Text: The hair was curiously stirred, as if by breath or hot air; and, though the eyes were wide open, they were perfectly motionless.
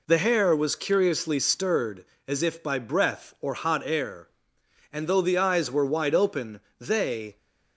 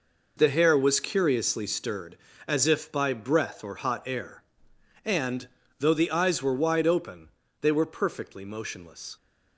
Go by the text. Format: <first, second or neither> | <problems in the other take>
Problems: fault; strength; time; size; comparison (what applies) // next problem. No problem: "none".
second | stops before "were perfectly motionless"; at 7.3 s